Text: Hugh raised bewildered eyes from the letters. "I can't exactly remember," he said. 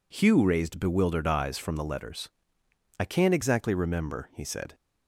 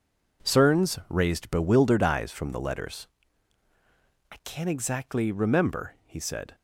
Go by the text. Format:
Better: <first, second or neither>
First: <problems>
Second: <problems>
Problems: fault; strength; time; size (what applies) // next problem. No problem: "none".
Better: first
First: none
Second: says "Cerns" for "Hugh"; at 0.4 s